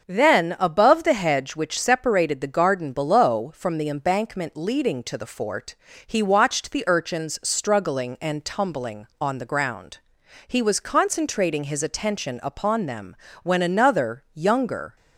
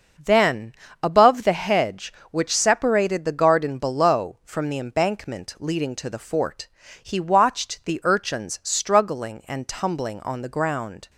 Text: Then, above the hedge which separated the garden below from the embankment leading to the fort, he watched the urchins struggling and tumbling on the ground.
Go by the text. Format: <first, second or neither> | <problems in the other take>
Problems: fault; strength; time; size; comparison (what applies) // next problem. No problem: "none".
second | starts louder than the rest; until 1.0 s; 6.5 dB; also in the second // goes on to say "He was concentrating his attention upon them when another younger"; strong; from 10.4 s on; 4.5 s long